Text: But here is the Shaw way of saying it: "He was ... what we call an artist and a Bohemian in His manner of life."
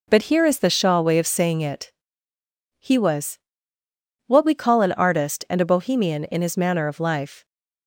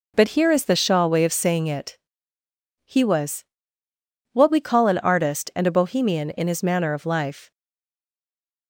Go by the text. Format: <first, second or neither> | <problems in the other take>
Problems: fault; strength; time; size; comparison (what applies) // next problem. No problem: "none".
first | stays silent after the last word; noticeable; from 7.5 s on; 1.1 s long